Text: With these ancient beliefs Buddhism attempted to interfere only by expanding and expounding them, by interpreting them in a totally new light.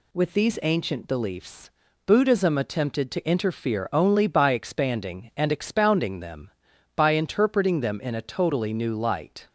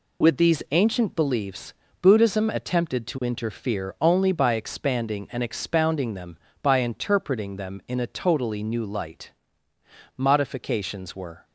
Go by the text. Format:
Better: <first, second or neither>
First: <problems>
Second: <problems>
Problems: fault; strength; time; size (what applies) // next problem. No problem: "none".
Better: first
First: pauses between "beliefs" and "Buddhism"; slight; at 1.7 s; 0.34 s long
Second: pauses between "beliefs" and "Buddhism"; slight; at 1.7 s; 0.26 s long // goes on to say "Modifications were"; noticeable; from 10.1 s on; 1.2 s long